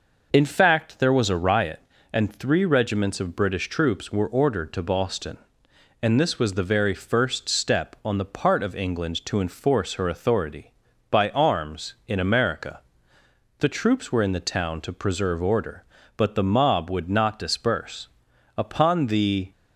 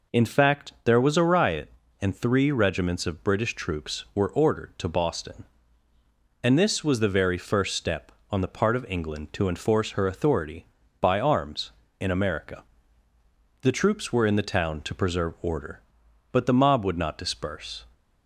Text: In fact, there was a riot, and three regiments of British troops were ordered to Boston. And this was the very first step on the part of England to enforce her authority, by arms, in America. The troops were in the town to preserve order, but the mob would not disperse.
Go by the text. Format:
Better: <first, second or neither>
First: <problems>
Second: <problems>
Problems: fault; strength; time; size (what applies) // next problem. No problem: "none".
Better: second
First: goes on to say "Upon the"; noticeable; from 18.5 s on; 0.94 s long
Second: none